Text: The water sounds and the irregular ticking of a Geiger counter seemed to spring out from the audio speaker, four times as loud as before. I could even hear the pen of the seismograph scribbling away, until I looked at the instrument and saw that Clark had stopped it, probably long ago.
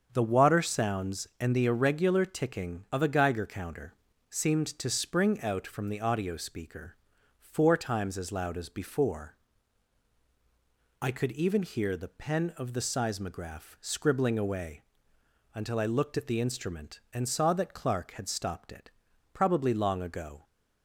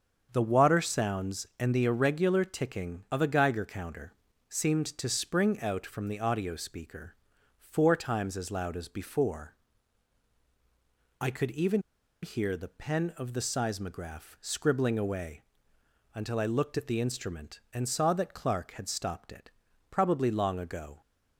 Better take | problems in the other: first | starts louder than the rest; until 1.3 s; 7 dB; also in the first // pauses between "counter" and "seemed"; at 4.1 s; 0.38 s long; also in the first // pauses between "even" and "hear"; at 11.7 s; 0.42 s long

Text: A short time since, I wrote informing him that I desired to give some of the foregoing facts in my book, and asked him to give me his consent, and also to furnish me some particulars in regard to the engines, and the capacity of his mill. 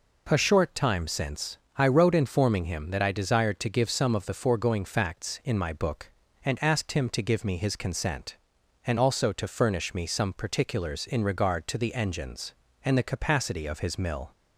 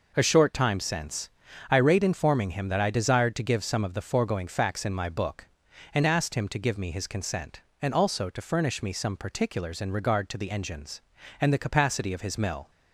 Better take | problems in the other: first | says "rate" for "wrote"; at 1.7 s

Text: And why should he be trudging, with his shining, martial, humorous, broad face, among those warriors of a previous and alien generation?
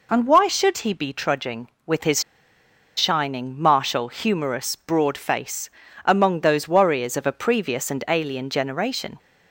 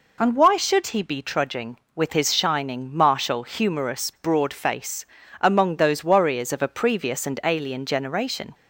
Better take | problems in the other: second | pauses between "his" and "shining"; noticeable; at 2.2 s; 0.75 s long

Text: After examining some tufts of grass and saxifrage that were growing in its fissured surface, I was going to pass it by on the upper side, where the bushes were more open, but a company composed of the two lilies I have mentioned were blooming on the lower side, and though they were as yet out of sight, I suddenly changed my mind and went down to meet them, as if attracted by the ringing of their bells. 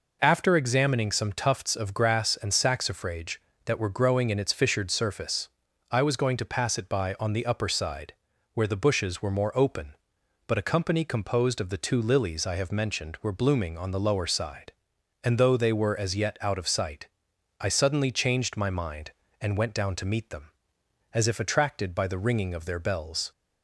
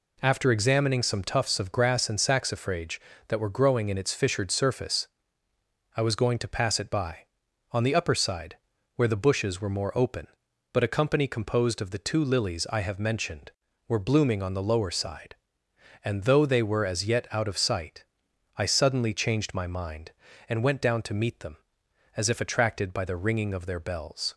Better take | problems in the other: neither | none

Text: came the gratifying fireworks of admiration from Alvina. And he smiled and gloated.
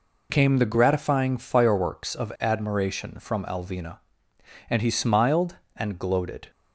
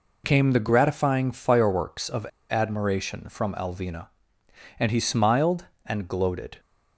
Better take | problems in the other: first | pauses between "of" and "admiration"; slight; at 2.2 s; 0.25 s long

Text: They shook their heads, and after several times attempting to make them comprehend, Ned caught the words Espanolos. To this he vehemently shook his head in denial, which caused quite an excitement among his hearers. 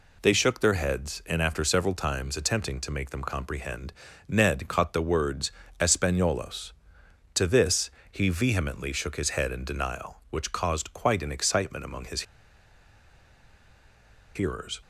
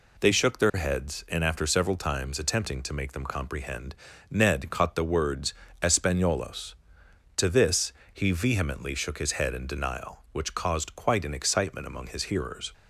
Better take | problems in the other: second | pauses between "words" and "Espanolos"; slight; at 5.5 s; 0.28 s long; slight in the second // pauses between "this" and "he"; slight; at 7.8 s; 0.22 s long; slight in the second // pauses between "his" and "hearers"; strong; at 12.2 s; 2.1 s long

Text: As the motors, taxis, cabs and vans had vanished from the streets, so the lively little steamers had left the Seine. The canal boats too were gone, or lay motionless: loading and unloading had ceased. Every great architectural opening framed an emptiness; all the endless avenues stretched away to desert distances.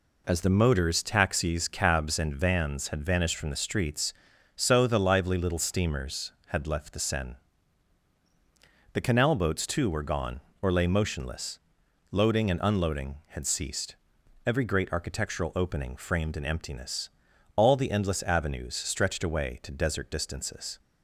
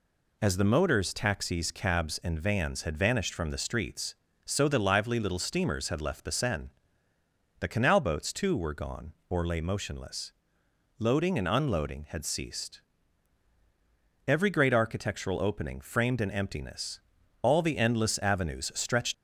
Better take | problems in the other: first | stops before "away to desert distances"; at 19.1 s

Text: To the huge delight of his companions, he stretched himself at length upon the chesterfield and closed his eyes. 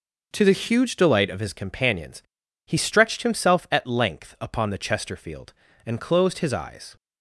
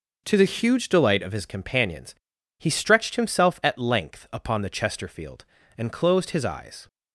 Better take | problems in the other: neither | none

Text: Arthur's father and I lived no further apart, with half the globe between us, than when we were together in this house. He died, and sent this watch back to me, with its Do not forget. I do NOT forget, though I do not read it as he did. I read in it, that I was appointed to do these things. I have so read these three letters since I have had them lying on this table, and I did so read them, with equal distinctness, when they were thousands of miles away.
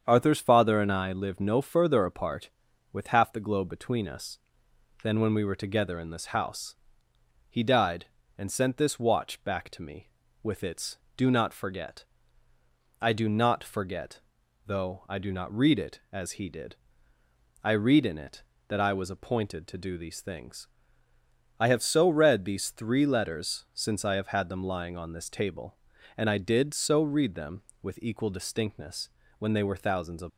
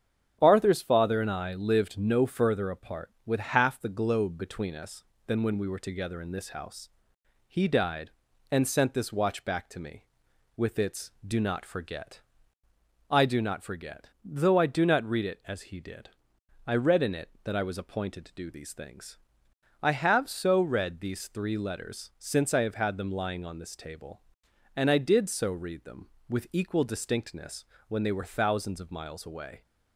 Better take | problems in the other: second | starts louder than the rest; strong; until 1.0 s; 7.5 dB; strong in the second // stops before "miles away"; at 30.2 s

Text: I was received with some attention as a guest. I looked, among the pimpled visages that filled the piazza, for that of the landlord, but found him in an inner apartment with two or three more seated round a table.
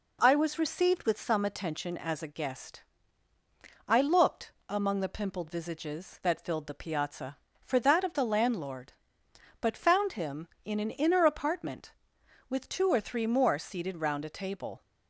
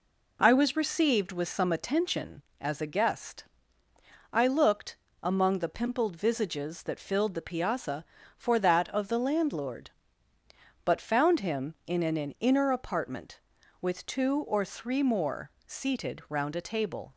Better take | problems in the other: first | says "an" twice; at 12.1 s // pauses between "more" and "seated"; slight; at 15.5 s; 0.16 s long

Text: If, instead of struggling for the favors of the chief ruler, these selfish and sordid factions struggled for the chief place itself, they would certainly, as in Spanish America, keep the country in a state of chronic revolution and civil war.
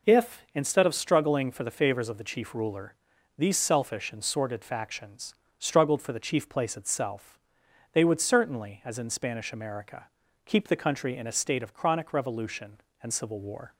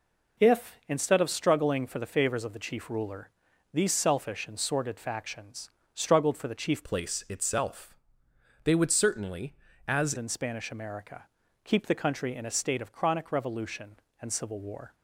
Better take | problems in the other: first | pauses between "factions" and "struggled"; slight; at 5.7 s; 0.24 s long; slight in the first // changes voice from "place" to "as"; from 6.8 to 10.1 s; 3.3 s long

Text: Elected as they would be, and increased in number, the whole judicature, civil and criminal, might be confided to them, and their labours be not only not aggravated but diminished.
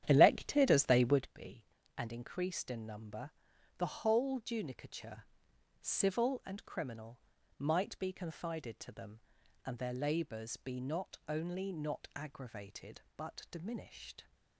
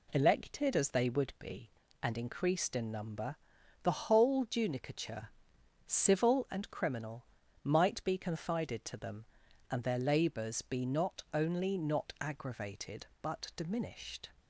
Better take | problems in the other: second | starts louder than the rest; strong; until 1.3 s; 10.5 dB

